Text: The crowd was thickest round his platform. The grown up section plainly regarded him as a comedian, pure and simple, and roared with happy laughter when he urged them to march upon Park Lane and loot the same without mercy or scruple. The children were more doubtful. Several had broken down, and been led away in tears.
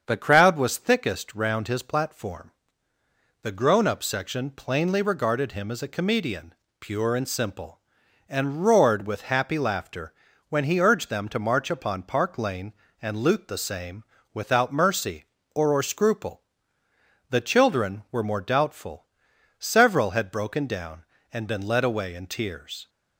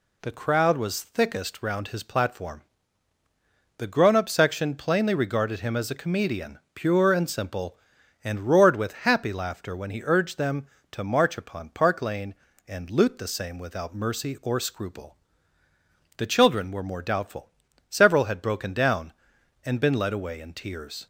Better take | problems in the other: second | starts louder than the rest; until 1.0 s; 7 dB // pauses between "laughter" and "when"; slight; at 10.1 s; 0.36 s long // pauses between "same" and "without"; slight; at 14.0 s; 0.30 s long // says "or" twice; at 15.7 s

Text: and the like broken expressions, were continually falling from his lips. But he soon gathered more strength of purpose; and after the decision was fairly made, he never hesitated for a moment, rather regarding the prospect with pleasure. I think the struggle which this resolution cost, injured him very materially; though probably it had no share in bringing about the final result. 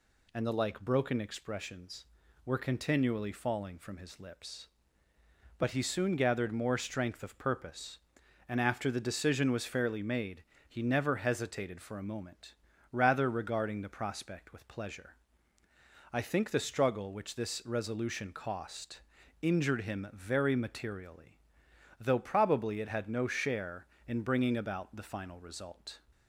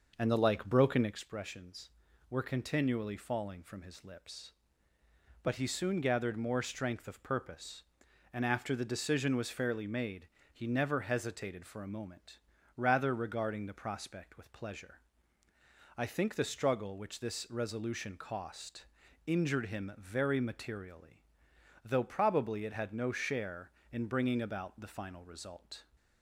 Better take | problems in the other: first | starts louder than the rest; noticeable; until 1.2 s; 6 dB

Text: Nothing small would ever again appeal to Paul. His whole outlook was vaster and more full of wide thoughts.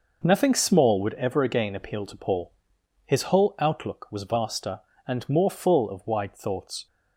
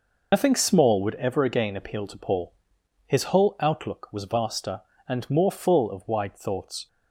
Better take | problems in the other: first | loses the start of "Nothing"; at 0.3 s; 100 ms

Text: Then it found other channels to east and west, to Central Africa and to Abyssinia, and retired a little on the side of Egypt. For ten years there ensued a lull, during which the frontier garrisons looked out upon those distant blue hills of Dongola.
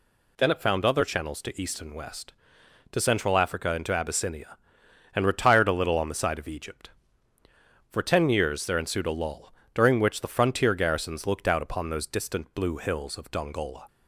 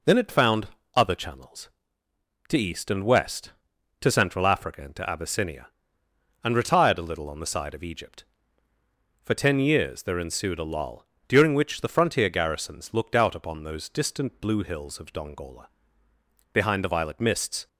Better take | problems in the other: first | pauses between "found" and "other"; slight; at 0.6 s; 0.28 s long // goes on to say "Behind the violet mists"; noticeable; from 16.5 s on; 1.1 s long

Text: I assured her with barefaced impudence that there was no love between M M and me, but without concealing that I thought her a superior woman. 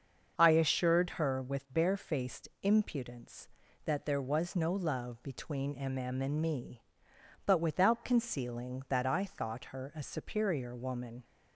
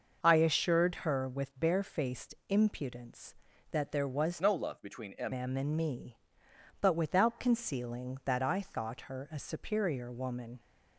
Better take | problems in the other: first | starts louder than the rest; noticeable; until 1.2 s; 6 dB; also in the first // changes voice from "no" to "M"; from 4.4 to 5.3 s; 0.9 s long

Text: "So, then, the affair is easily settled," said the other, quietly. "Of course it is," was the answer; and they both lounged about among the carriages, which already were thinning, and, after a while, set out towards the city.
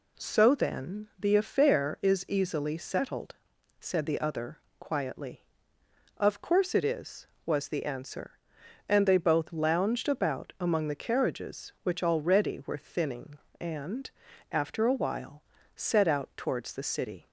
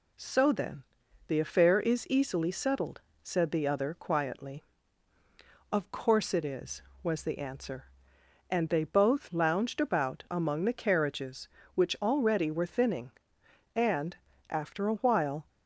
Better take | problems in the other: first | stops before "set out towards the city"; at 15.4 s

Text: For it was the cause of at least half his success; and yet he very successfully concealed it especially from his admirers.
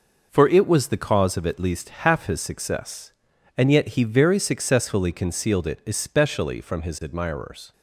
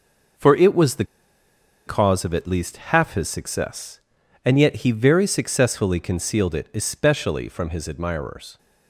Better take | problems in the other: first | pauses between "the" and "cause"; noticeable; at 1.0 s; 0.83 s long

